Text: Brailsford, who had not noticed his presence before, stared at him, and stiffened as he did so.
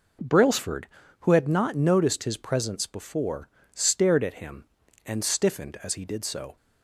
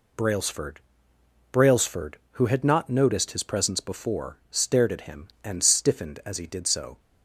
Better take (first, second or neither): first